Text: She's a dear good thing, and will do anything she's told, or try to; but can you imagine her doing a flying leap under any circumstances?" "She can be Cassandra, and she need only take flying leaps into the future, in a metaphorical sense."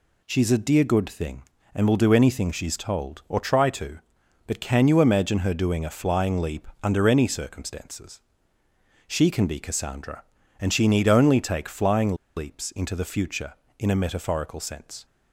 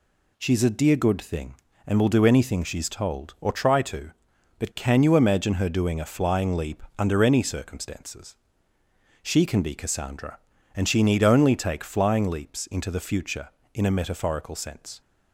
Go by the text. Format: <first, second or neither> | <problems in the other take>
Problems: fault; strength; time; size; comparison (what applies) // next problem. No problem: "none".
second | pauses between "flying" and "leaps"; slight; at 12.1 s; 0.21 s long